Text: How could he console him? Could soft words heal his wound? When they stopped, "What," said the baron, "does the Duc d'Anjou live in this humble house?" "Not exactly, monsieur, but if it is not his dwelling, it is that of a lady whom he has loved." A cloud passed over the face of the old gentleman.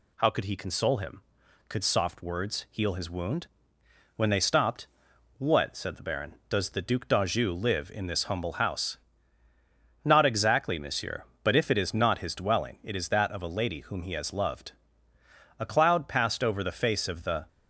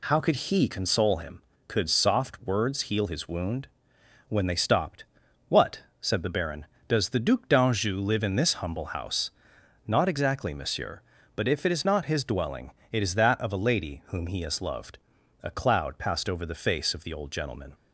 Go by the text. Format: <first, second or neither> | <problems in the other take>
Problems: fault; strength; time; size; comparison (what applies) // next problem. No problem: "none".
second | stops before "old gentleman"; at 17.4 s